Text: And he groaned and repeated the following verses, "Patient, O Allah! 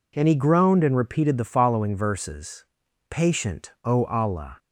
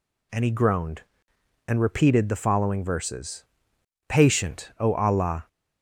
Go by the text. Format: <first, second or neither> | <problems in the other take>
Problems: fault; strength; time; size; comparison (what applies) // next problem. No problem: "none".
neither | none